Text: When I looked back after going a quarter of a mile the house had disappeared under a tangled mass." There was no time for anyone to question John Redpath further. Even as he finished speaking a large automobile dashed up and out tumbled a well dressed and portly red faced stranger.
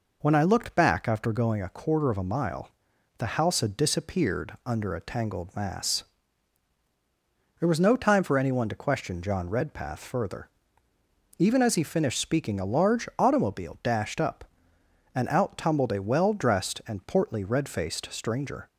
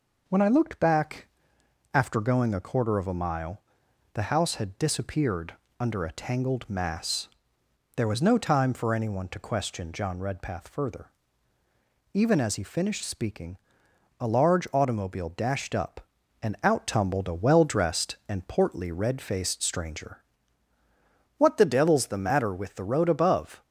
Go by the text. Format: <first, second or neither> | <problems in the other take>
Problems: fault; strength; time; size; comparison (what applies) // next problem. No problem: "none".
first | pauses between "back" and "after"; noticeable; at 1.2 s; 0.66 s long // pauses between "mile" and "the"; noticeable; at 3.6 s; 0.52 s long; noticeable in the first // pauses between "disappeared" and "under"; slight; at 5.5 s; 0.24 s long // pauses between "speaking" and "a"; noticeable; at 13.5 s; 0.64 s long // goes on to say "What the devil's the matter with the road above"; strong; from 21.3 s on; 2.2 s long